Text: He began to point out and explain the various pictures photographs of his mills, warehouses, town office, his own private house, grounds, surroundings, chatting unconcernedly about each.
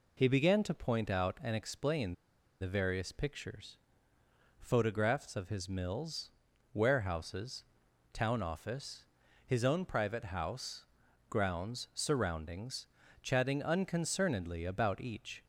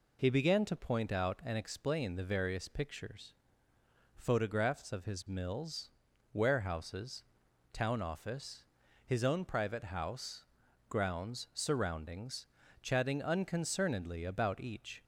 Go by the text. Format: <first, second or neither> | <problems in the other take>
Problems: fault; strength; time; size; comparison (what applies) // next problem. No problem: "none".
second | pauses between "explain" and "the"; noticeable; at 2.1 s; 0.46 s long // pauses between "pictures" and "photographs"; noticeable; at 3.7 s; 0.82 s long; noticeable in the second